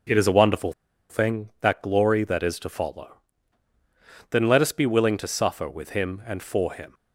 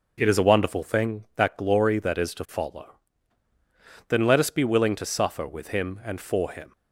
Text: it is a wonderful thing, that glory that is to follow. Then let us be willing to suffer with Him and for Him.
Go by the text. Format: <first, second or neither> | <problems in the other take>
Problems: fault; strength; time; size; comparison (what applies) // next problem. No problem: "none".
second | pauses between "wonderful" and "thing"; at 0.7 s; 0.37 s long